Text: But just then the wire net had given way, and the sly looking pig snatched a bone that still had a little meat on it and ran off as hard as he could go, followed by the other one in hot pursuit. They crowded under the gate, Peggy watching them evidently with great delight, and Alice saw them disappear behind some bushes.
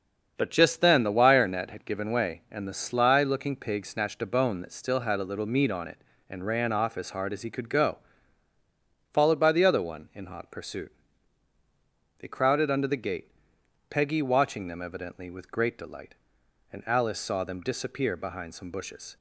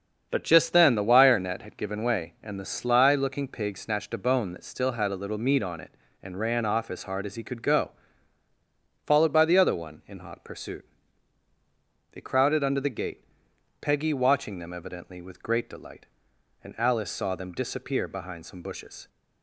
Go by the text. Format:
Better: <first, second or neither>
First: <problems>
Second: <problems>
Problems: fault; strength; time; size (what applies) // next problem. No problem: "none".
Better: neither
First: starts louder than the rest; until 1.3 s; 7 dB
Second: starts louder than the rest; until 1.3 s; 7 dB